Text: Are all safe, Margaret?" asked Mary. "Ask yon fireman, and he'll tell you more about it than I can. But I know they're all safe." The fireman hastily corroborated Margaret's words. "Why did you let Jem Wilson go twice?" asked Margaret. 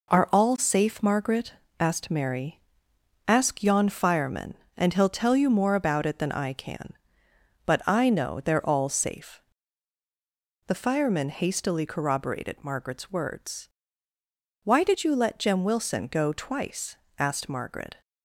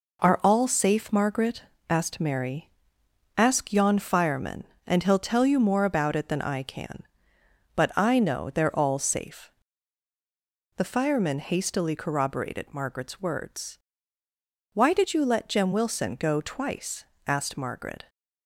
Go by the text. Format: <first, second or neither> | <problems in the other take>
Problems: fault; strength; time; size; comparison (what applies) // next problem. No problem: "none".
neither | none